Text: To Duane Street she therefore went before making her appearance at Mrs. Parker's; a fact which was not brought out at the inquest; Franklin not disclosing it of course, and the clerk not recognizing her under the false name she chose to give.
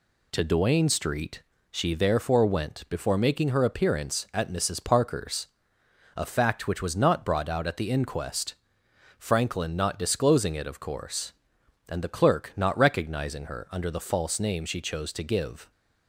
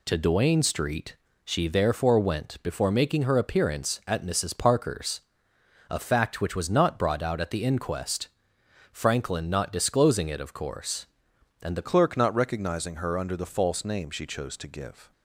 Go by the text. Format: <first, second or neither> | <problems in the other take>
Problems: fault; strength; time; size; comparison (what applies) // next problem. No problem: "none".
first | pauses between "Street" and "she"; slight; at 1.1 s; 0.28 s long; slight in the first // changes voice at "clerk"; from 11.8 s on; 3.3 s long